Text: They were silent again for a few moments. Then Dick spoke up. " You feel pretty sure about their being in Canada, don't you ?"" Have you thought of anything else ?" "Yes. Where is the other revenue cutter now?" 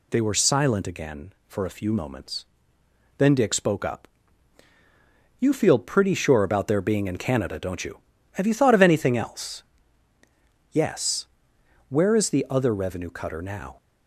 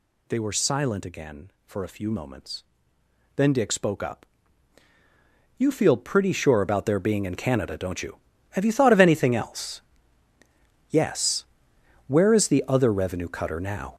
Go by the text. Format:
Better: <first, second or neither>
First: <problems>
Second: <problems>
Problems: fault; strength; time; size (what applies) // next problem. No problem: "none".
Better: first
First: none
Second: gets louder; noticeable; throughout; 6 dB